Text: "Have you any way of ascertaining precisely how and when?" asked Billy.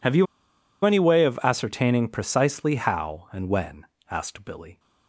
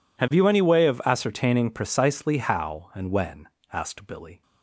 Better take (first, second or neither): second